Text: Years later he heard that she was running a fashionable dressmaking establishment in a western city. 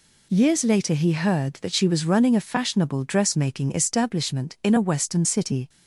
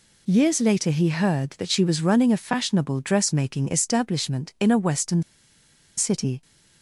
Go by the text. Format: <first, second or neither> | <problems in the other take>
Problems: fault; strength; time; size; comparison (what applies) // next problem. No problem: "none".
first | pauses between "western" and "city"; noticeable; at 5.2 s; 0.76 s long